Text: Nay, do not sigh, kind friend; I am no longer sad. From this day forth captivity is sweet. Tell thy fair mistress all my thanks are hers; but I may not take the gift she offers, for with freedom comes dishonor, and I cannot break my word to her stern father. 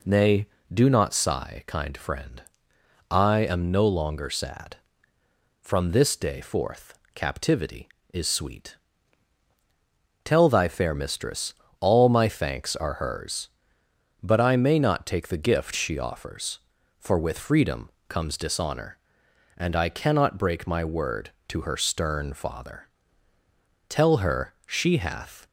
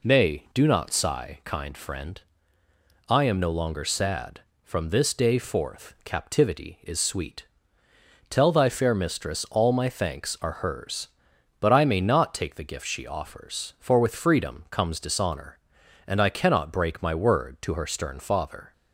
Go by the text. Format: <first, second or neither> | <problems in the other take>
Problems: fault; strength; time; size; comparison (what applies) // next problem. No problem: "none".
second | pauses between "forth" and "captivity"; slight; at 6.9 s; 0.18 s long // pauses between "mistress" and "all"; slight; at 11.5 s; 0.26 s long // pauses between "freedom" and "comes"; slight; at 17.9 s; 0.16 s long // goes on to say "Tell her she hath"; from 23.8 s on; 1.5 s long